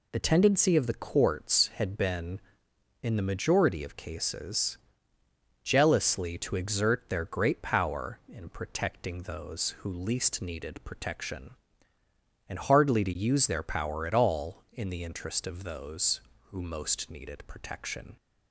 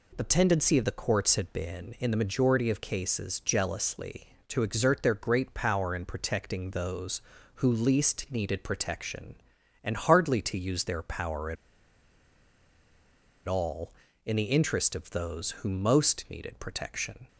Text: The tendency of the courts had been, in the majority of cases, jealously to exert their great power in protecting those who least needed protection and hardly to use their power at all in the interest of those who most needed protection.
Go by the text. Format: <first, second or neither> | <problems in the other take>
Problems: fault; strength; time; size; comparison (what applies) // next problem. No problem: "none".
first | pauses between "at" and "all"; strong; at 11.5 s; 1.9 s long